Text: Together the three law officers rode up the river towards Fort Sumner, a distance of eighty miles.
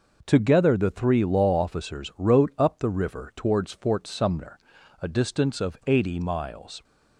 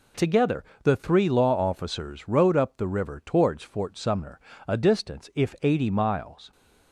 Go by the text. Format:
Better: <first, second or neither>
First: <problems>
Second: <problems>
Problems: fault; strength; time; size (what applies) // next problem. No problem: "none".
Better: first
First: none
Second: pauses between "Together" and "the"; slight; at 0.6 s; 0.20 s long // says "if" for "of"; at 5.3 s